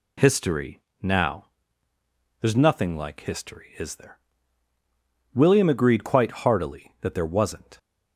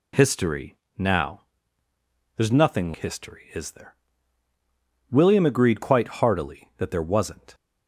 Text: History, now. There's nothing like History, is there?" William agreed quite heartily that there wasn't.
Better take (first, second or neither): first